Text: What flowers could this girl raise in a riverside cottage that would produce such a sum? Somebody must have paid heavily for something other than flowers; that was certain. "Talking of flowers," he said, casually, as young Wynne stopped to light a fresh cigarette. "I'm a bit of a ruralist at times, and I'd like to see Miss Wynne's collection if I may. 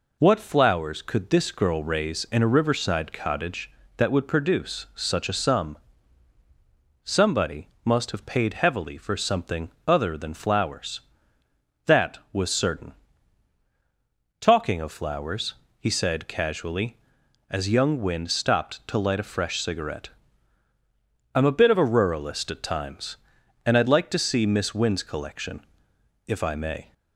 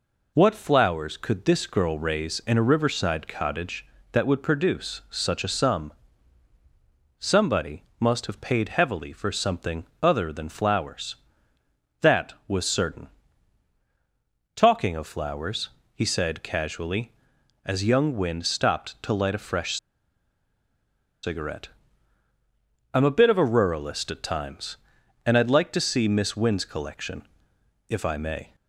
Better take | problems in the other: first | pauses between "Somebody" and "must"; slight; at 7.8 s; 0.16 s long; slight in the first // pauses between "something" and "other"; slight; at 9.8 s; 0.16 s long; slight in the first // pauses between "fresh" and "cigarette"; strong; at 19.7 s; 1.4 s long // pauses between "collection" and "if"; noticeable; at 27.2 s; 0.60 s long; noticeable in the first

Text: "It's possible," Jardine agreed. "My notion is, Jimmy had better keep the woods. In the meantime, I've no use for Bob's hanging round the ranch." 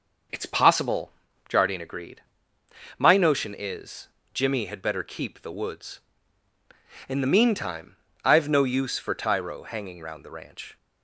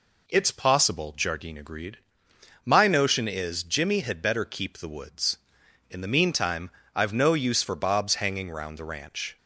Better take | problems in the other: second | says "Tyro" for "Bob's"; at 9.1 s

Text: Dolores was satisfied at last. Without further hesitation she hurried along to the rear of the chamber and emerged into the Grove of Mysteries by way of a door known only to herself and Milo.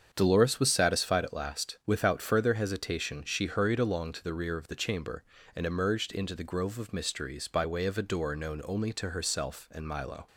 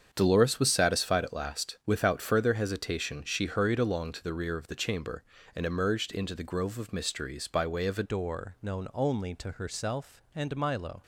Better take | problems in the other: first | starts louder than the rest; strong; until 1.1 s; 7.5 dB; strong in the first // changes voice at "door"; from 8.0 s on; 3.0 s long

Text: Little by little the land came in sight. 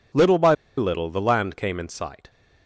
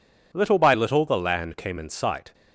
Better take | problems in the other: second | pauses between "by" and "little"; slight; at 0.5 s; 0.24 s long

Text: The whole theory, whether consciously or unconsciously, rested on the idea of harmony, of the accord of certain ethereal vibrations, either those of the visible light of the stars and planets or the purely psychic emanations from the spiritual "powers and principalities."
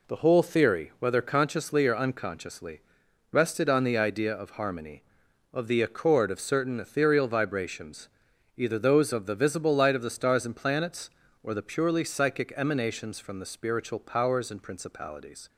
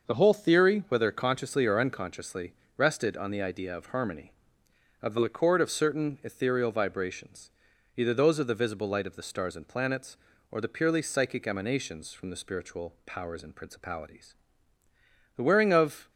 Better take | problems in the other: first | starts louder than the rest; noticeable; until 1.1 s; 6 dB // goes on to say "The wearing of"; noticeable; from 15.3 s on; 0.74 s long

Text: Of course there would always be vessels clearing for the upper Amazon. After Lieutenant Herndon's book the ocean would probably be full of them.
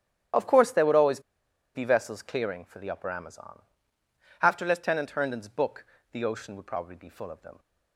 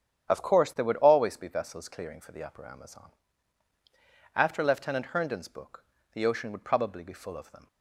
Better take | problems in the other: second | starts louder than the rest; strong; until 1.8 s; 10 dB; strong in the second // pauses between "always" and "be"; noticeable; at 1.2 s; 0.54 s long // pauses between "book" and "the"; slight; at 5.8 s; 0.30 s long; slight in the second

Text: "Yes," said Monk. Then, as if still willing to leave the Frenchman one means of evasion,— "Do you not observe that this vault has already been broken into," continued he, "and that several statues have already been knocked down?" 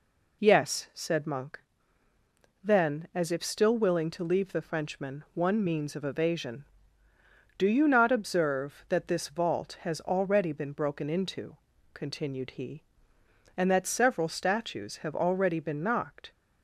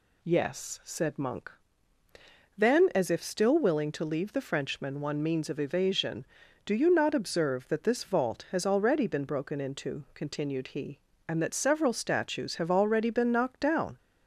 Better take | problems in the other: second | stops before "down"; at 16.3 s

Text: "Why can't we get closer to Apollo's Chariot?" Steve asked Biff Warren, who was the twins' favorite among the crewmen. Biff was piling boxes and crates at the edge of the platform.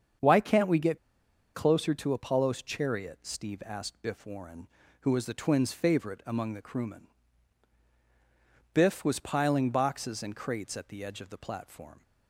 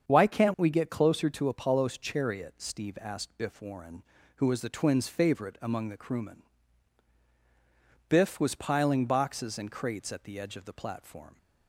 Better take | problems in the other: second | starts louder than the rest; strong; until 1.7 s; 7.5 dB; strong in the second // pauses between "get" and "closer"; noticeable; at 0.9 s; 0.56 s long

